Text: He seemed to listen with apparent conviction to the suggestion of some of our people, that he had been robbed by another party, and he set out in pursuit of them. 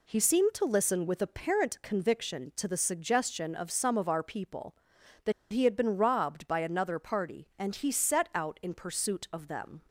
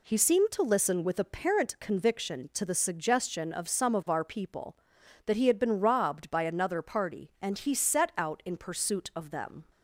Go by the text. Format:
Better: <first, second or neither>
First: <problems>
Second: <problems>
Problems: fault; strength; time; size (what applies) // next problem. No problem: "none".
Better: second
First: pauses between "that" and "he"; slight; at 5.3 s; 0.19 s long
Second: none